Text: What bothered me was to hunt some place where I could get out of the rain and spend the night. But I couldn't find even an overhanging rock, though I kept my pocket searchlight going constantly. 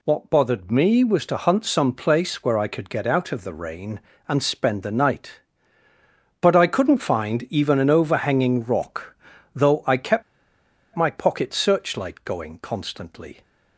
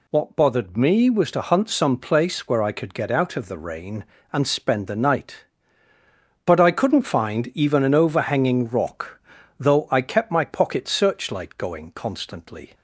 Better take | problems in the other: second | pauses between "kept" and "my"; noticeable; at 10.2 s; 0.72 s long

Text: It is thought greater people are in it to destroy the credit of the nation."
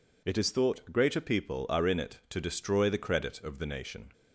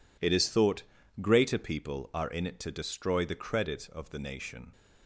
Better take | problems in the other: first | gets quieter; strong; throughout; 13.5 dB // pauses between "thought" and "greater"; at 0.8 s; 0.40 s long

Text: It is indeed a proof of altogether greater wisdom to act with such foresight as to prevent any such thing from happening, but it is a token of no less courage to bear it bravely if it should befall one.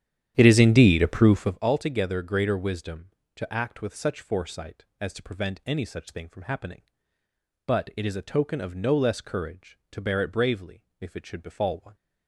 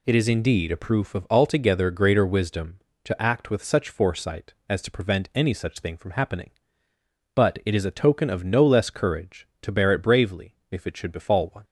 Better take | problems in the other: second | starts louder than the rest; strong; until 1.6 s; 10.5 dB

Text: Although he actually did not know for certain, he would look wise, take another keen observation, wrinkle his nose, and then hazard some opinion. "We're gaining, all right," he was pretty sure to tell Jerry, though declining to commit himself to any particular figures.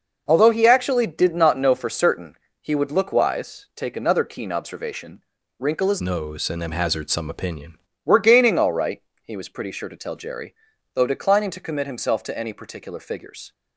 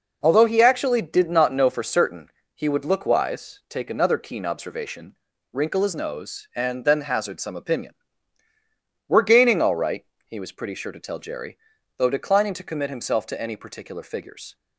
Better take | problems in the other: second | changes voice from "nose" to "opinion"; from 6.0 to 7.7 s; 1.7 s long

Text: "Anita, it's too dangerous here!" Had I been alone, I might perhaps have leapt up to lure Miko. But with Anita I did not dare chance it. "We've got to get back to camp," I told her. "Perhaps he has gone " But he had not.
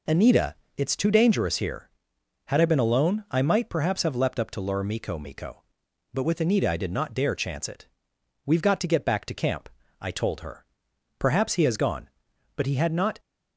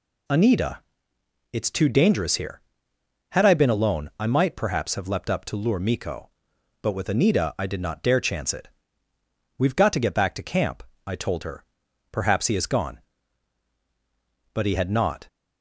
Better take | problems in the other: second | says "Miko" twice; at 5.1 s

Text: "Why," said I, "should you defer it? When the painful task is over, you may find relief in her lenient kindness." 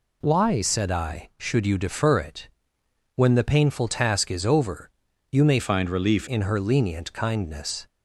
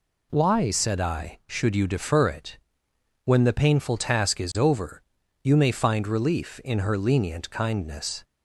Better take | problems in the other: second | changes voice from "find" to "relief"; from 5.5 to 6.2 s; 0.7 s long

